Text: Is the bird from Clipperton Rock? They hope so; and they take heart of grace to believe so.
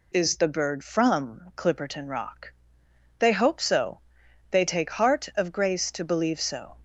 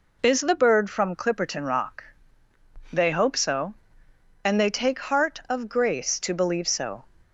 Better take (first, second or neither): second